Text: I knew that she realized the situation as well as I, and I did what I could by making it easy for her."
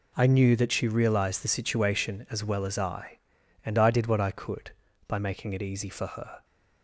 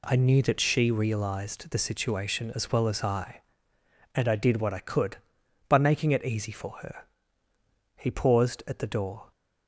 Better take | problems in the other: first | goes on to say "He paused at the door"; from 7.9 s on; 1.3 s long

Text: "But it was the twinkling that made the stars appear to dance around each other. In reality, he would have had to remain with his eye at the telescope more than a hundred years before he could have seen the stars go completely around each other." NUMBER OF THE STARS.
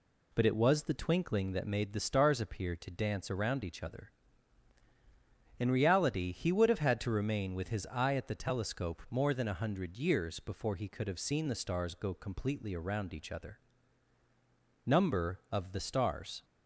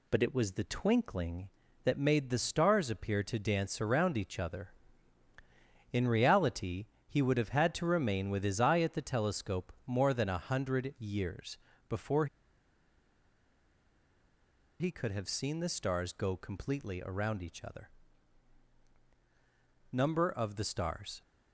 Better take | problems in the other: first | pauses between "years" and "before"; slight; at 11.5 s; 0.32 s long // pauses between "before" and "he"; strong; at 12.2 s; 2.5 s long

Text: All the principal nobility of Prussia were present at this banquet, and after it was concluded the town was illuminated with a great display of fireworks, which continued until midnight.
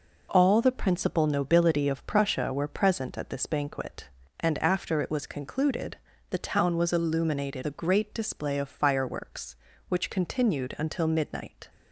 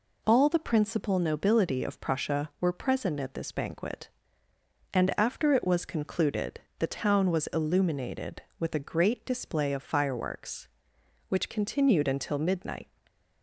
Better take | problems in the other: second | pauses between "concluded" and "the"; slight; at 5.9 s; 0.34 s long; slight in the second // skips "with"; at 7.6 s

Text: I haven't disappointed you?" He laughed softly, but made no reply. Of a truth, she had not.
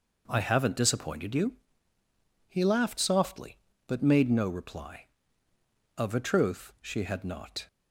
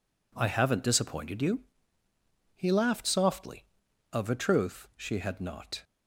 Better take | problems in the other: first | skips "but made no reply"; at 3.8 s

